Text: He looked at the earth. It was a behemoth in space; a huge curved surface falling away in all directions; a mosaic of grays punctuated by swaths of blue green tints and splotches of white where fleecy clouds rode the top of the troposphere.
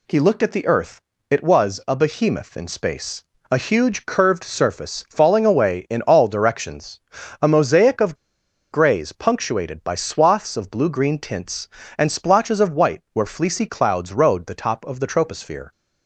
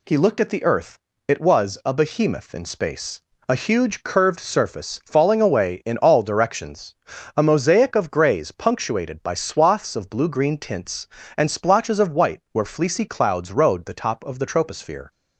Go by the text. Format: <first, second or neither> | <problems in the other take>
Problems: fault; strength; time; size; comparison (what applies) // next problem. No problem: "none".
second | pauses between "of" and "grays"; noticeable; at 8.1 s; 0.56 s long